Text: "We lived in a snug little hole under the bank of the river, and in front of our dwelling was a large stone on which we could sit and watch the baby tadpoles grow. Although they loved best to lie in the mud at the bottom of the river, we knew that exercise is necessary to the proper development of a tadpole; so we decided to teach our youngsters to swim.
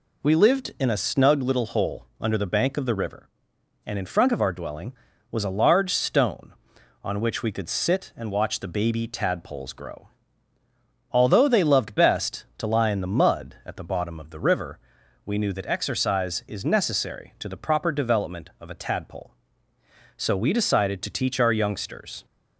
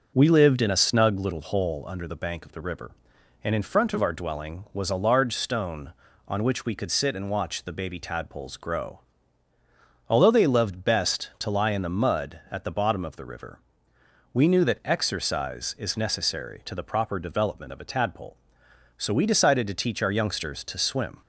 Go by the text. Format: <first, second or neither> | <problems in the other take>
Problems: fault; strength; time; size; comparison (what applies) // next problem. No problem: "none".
second | stops before "to swim"; at 22.2 s